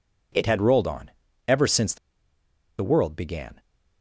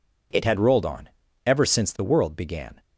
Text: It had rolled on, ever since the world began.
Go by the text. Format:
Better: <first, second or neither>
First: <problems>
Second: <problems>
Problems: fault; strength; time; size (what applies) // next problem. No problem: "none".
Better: second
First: pauses between "the" and "world"; noticeable; at 1.9 s; 0.83 s long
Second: none